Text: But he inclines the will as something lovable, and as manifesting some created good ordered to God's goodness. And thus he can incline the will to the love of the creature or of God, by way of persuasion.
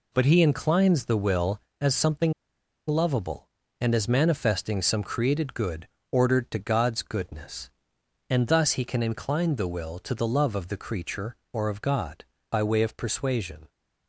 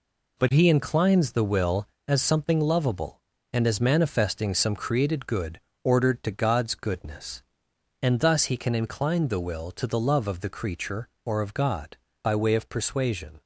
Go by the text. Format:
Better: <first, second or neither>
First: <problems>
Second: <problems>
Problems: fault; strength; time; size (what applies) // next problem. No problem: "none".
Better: second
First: pauses between "something" and "lovable"; noticeable; at 2.3 s; 0.55 s long // pauses between "good" and "ordered"; slight; at 5.8 s; 0.24 s long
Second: pauses between "good" and "ordered"; slight; at 5.5 s; 0.24 s long